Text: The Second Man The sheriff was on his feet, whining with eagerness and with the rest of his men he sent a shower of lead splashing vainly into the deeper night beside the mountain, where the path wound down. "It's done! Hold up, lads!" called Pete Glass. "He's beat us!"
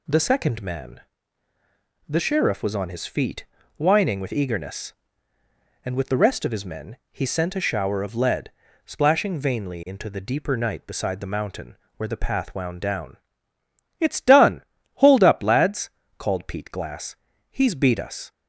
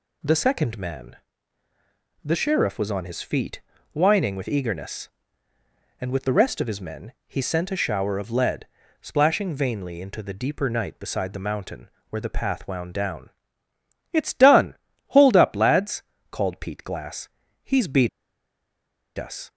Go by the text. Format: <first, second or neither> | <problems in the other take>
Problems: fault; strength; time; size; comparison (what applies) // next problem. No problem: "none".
first | pauses between "Man" and "The"; at 1.1 s; 1.0 s long; also in the first // pauses between "men" and "he"; slight; at 7.1 s; 0.16 s long; slight in the first // pauses between "lead" and "splashing"; slight; at 8.6 s; 0.36 s long; slight in the first // pauses between "beat" and "us"; at 18.0 s; 1.0 s long